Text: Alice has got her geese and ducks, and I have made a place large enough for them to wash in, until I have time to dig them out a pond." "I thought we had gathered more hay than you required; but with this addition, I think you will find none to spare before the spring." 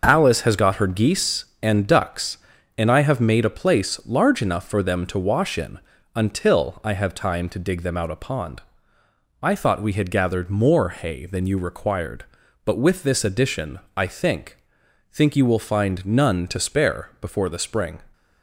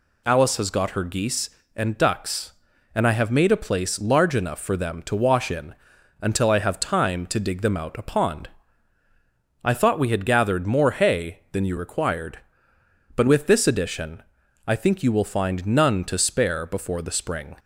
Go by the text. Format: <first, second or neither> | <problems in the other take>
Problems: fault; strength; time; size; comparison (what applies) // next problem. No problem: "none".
second | starts louder than the rest; noticeable; until 1.0 s; 6 dB // says "think" twice; at 15.1 s